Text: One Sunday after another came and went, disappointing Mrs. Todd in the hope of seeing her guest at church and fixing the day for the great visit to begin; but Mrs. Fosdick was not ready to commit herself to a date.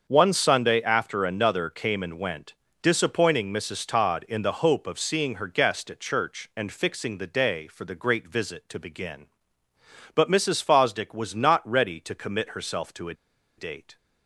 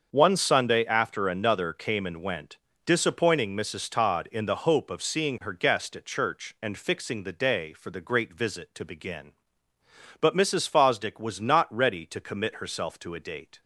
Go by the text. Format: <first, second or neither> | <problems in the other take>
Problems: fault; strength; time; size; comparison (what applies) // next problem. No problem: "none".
second | starts louder than the rest; until 1.1 s; 6.5 dB; also in the second // pauses between "a" and "date"; at 13.1 s; 0.44 s long